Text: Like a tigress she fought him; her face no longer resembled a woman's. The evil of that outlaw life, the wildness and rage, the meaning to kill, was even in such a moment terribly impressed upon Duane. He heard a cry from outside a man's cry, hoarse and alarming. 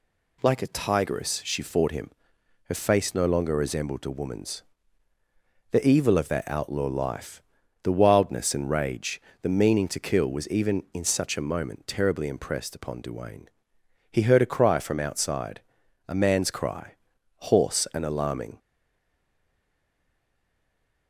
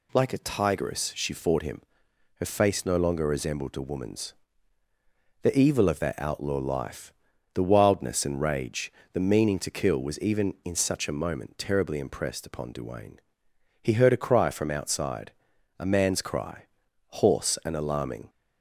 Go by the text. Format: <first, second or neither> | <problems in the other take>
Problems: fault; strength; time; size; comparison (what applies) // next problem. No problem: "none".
second | pauses between "outside" and "a"; noticeable; at 15.6 s; 0.50 s long; noticeable in the second // stays silent after the last word; from 18.5 s on; 2.5 s long